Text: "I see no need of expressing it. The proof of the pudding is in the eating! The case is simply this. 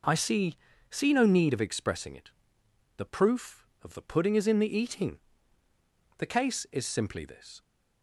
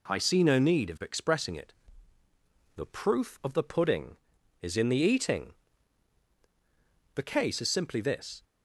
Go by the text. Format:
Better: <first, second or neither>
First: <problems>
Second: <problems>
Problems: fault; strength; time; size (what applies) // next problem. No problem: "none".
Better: second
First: says "see" twice; at 0.9 s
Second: none